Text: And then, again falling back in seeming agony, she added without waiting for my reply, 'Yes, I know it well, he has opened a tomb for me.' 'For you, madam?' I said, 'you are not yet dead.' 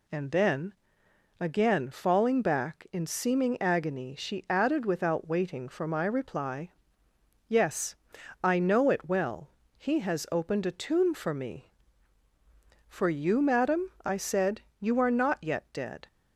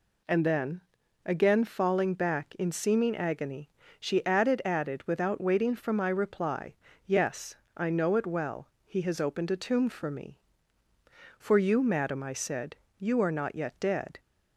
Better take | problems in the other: first | says "added" twice; at 4.6 s

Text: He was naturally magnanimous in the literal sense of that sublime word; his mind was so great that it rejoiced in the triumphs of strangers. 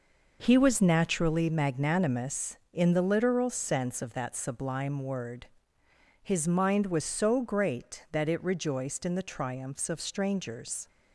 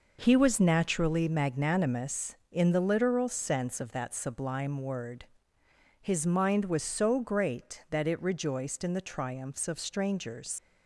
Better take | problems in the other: first | leaves "strangers" unfinished; at 10.5 s; 70 ms

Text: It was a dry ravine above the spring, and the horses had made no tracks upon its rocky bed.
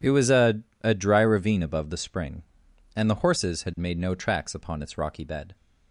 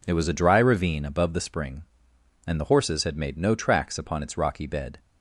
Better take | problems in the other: second | says "a" twice; at 0.8 s

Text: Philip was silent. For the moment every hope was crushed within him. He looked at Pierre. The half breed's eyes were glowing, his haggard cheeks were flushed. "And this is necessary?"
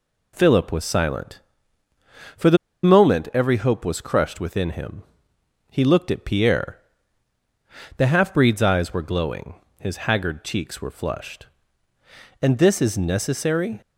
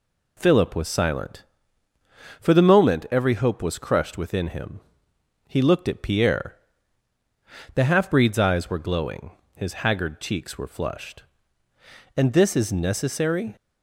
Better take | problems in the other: second | pauses between "the" and "moment"; slight; at 2.5 s; 0.27 s long

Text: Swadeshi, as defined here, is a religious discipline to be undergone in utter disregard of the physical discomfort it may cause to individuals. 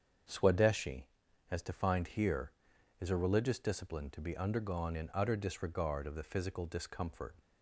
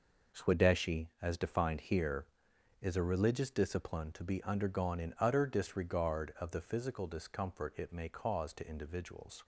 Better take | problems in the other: second | starts louder than the rest; strong; until 1.7 s; 7 dB // stops before "it may cause to individuals"; at 7.3 s

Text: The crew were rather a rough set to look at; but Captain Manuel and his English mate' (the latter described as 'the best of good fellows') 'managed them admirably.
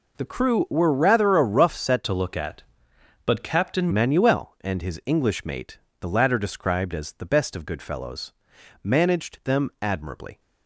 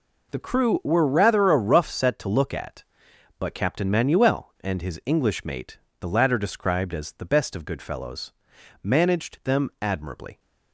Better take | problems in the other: second | changes voice from "to" to "Captain"; from 2.0 to 3.8 s; 1.8 s long

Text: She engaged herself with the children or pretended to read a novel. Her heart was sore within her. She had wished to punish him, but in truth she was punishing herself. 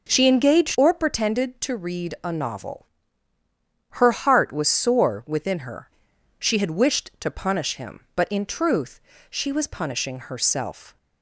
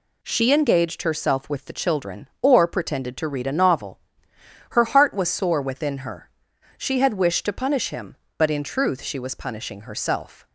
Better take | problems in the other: second | skips "herself with the children"; at 0.7 s // pauses between "truth" and "she"; slight; at 8.9 s; 0.32 s long

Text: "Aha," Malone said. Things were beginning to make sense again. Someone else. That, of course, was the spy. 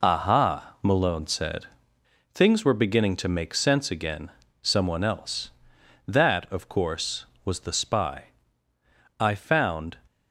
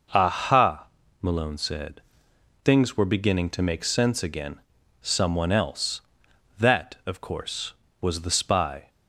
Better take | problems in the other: second | goes on to say "I found"; noticeable; from 9.1 s on; 0.80 s long

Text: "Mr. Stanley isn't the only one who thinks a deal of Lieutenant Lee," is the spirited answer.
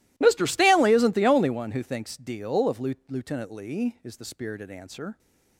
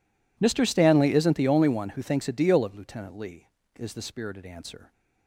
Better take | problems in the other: second | skips "a"; at 2.1 s

